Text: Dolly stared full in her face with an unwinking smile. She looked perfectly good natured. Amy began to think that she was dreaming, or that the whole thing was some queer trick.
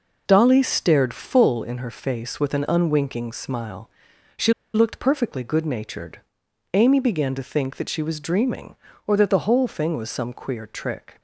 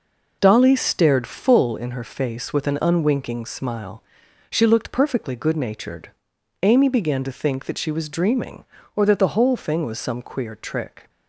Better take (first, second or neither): second